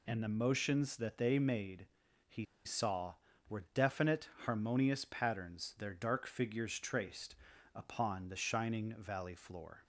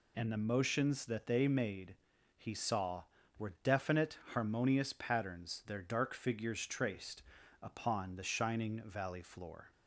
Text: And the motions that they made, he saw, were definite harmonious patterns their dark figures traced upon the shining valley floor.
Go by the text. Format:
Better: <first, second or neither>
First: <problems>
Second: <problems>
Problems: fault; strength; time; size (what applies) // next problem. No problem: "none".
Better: second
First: pauses between "he" and "saw"; slight; at 2.4 s; 0.20 s long // pauses between "definite" and "harmonious"; slight; at 4.2 s; 0.16 s long // pauses between "traced" and "upon"; at 7.3 s; 0.40 s long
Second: pauses between "traced" and "upon"; at 7.2 s; 0.40 s long